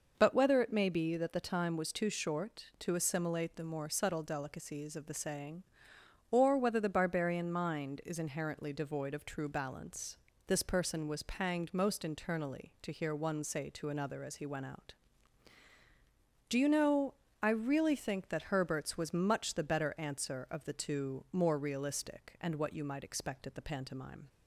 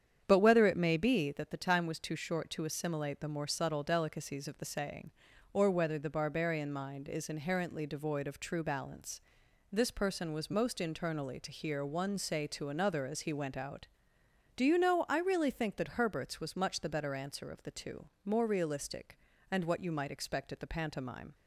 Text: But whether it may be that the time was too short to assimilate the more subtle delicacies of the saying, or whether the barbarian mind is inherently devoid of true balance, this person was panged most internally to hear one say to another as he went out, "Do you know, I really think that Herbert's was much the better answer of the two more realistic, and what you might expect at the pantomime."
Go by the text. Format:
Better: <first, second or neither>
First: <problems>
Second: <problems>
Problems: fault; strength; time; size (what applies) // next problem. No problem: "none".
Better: first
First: none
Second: starts louder than the rest; strong; until 1.2 s; 8.5 dB // skips "panged"; at 10.5 s // pauses between "two" and "more"; slight; at 18.0 s; 0.16 s long